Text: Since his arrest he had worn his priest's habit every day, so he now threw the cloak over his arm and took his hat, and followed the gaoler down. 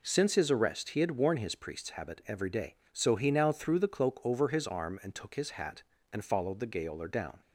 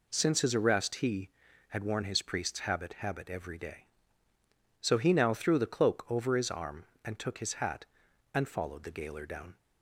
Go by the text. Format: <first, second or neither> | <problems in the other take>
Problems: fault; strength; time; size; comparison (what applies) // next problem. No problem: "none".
first | says "habit" twice; at 2.9 s